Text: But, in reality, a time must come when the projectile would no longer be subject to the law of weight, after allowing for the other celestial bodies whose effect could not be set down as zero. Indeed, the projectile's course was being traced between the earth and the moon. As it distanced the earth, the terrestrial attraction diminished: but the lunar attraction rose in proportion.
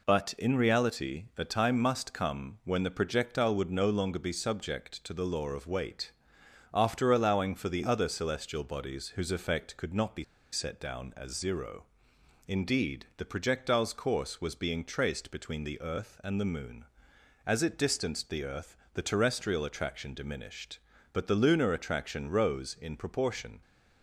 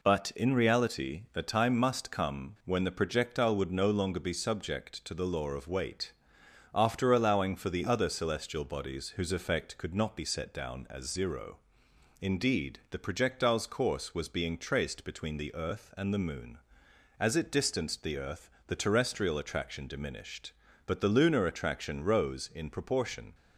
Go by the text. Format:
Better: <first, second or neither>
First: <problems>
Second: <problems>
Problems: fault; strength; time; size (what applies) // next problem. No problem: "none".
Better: second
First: pauses between "be" and "set"; slight; at 10.2 s; 0.28 s long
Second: none